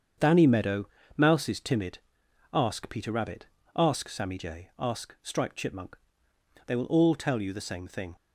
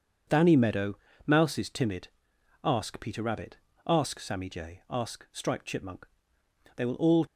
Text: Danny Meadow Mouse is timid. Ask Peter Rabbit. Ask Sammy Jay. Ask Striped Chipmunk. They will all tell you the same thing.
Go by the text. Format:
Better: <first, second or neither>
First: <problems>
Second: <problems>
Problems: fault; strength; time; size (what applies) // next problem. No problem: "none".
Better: first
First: starts louder than the rest; strong; until 1.4 s; 7.5 dB // pauses between "Meadow" and "Mouse"; slight; at 0.8 s; 0.28 s long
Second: starts louder than the rest; until 1.5 s; 7 dB // pauses between "Meadow" and "Mouse"; slight; at 0.9 s; 0.28 s long // stops before "tell you the same thing"; at 7.2 s